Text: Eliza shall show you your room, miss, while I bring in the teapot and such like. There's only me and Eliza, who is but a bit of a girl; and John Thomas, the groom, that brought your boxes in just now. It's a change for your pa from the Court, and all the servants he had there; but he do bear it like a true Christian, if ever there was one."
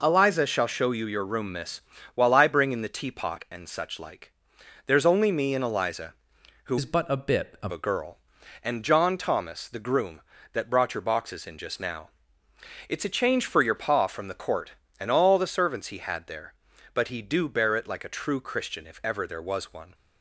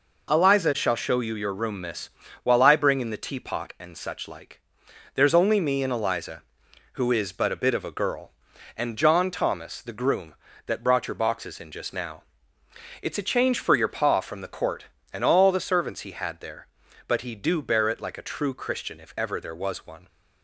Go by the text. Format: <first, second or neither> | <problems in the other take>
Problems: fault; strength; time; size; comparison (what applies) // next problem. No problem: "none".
second | changes voice from "is" to "of"; from 6.7 to 7.7 s; 1.0 s long